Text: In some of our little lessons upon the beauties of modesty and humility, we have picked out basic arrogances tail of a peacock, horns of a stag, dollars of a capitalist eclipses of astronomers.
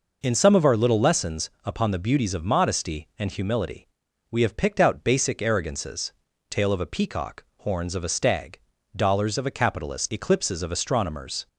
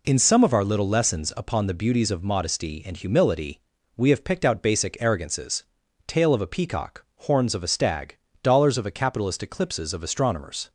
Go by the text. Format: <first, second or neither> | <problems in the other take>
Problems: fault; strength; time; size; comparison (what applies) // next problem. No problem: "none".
neither | pauses between "arrogances" and "tail"; the same in both